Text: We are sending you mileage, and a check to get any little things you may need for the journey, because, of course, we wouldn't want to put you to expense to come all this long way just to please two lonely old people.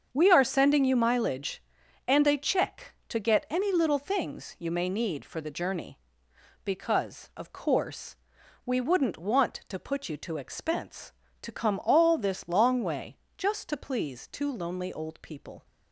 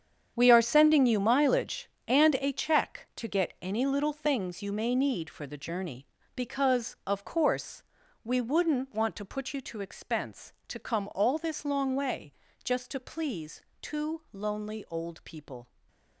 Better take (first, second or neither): first